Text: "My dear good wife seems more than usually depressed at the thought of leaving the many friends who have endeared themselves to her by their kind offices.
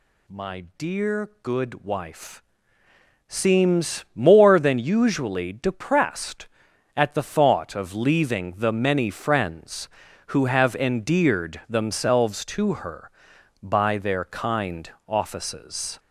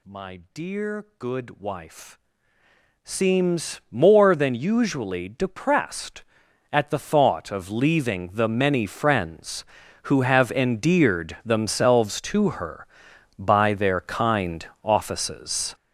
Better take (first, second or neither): first